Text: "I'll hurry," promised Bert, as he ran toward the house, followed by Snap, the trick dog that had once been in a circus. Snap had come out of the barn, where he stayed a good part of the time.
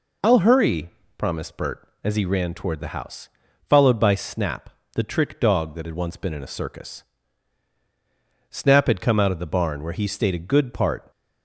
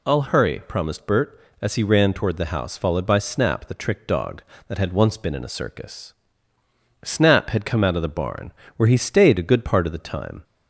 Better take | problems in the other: second | stops before "of the time"; at 11.1 s

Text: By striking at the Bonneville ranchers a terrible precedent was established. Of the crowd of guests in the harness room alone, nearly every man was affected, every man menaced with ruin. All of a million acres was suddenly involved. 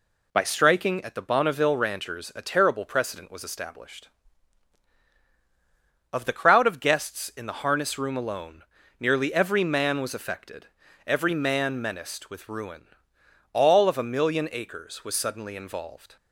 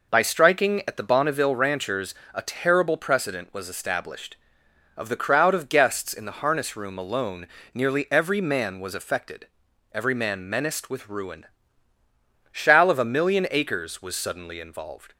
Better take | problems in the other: first | pauses between "ranchers" and "a"; slight; at 2.1 s; 0.18 s long // says "Shall" for "All"; at 12.5 s

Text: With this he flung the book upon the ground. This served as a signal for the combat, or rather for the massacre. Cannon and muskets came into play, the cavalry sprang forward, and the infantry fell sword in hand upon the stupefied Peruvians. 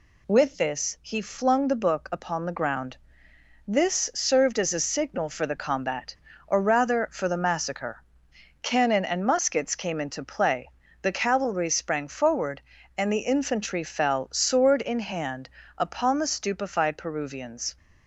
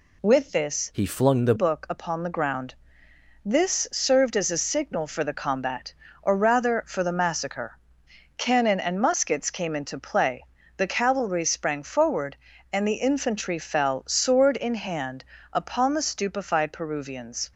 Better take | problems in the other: first | changes voice from "he" to "the"; from 0.9 to 1.5 s; 0.6 s long // pauses between "hand" and "upon"; slight; at 15.2 s; 0.30 s long; slight in the first

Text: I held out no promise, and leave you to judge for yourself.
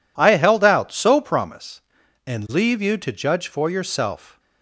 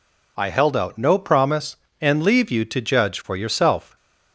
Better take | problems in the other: second | says "so" for "no"; at 0.9 s

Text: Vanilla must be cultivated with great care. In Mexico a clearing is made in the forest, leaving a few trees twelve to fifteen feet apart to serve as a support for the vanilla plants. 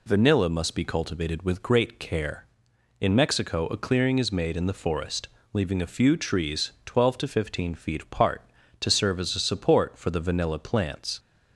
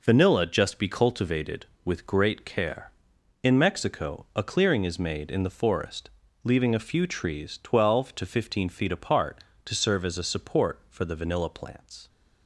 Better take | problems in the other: first | says "just" for "must"; at 0.4 s

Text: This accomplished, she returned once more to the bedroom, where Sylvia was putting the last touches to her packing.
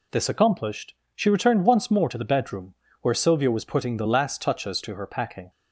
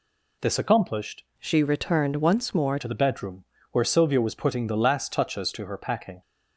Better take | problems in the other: first | changes voice from "she" to "more"; from 1.3 to 2.7 s; 1.4 s long

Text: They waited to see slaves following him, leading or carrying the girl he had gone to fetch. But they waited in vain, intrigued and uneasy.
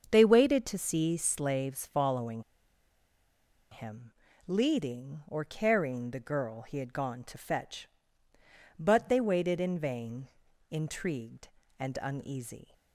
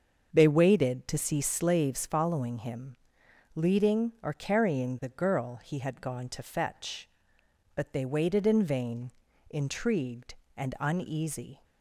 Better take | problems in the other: second | starts louder than the rest; until 1.1 s; 7 dB; also in the second // pauses between "following" and "him"; strong; at 2.4 s; 1.2 s long

